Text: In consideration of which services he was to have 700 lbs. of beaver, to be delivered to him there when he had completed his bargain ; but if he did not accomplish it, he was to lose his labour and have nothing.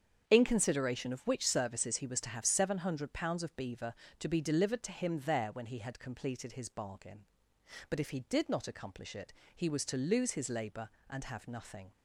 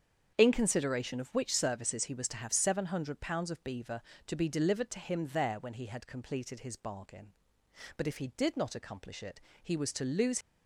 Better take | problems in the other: first | starts louder than the rest; strong; until 1.4 s; 8 dB; strong in the first // stops before "his labour and have nothing"; at 10.4 s

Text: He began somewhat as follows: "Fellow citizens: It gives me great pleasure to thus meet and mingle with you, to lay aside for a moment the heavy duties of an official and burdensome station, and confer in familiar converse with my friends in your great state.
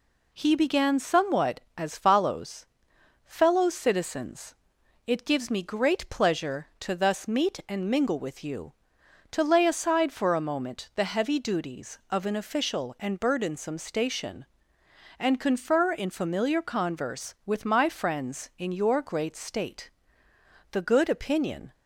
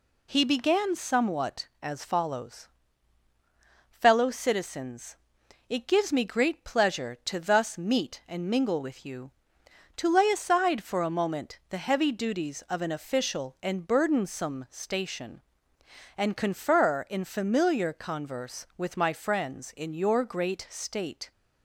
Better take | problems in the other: second | goes on to say "The good opinion"; noticeable; from 20.7 s on; 1.0 s long

